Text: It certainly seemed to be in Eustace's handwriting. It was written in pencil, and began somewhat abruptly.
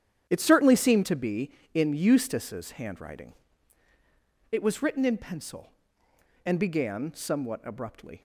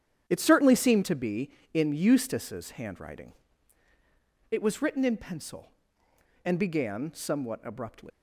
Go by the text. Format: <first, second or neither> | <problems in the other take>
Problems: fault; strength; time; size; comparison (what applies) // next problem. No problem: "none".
first | starts louder than the rest; strong; until 1.2 s; 9.5 dB; strong in the first // leaves "abruptly" unfinished; at 8.1 s; 105 ms